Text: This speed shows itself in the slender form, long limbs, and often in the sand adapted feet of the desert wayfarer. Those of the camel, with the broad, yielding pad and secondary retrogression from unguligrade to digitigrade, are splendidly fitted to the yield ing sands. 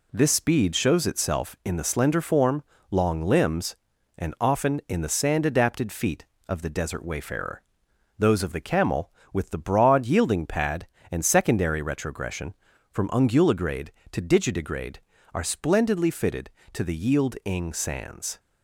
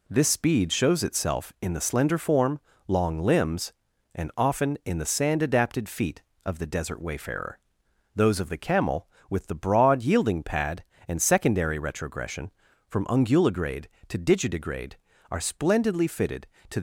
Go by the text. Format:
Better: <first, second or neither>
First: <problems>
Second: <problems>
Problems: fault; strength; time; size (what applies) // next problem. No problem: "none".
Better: first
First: none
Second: stops before "the yield ing sands"; at 16.7 s